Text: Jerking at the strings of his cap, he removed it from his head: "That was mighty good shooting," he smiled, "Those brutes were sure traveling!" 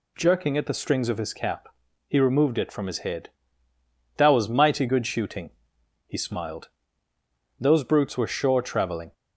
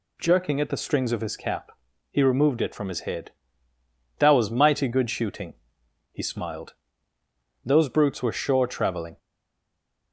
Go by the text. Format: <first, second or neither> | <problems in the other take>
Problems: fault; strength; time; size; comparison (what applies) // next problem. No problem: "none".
first | stays silent after the last word; slight; from 9.1 s on; 1.0 s long